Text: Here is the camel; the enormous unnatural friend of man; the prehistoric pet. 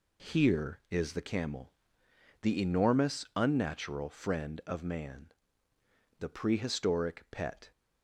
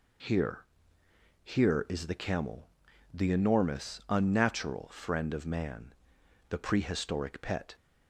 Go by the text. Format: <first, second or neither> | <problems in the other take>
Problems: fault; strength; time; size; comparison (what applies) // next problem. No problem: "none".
first | says "Here" twice; at 1.4 s